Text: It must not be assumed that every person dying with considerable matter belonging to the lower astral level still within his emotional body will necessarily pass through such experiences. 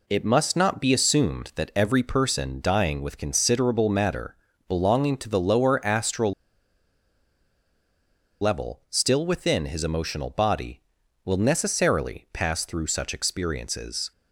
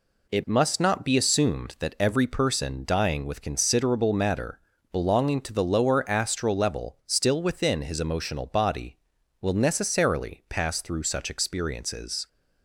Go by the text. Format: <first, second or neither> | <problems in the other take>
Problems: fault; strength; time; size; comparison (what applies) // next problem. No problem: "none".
second | pauses between "matter" and "belonging"; slight; at 4.3 s; 0.32 s long; slight in the second // pauses between "astral" and "level"; strong; at 6.3 s; 2.0 s long